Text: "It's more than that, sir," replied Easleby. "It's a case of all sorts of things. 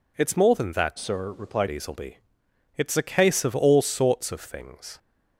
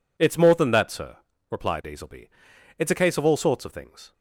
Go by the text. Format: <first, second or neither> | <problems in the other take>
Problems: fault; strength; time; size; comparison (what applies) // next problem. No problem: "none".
second | changes voice from "sir" to "replied"; from 0.9 to 1.6 s; 0.7 s long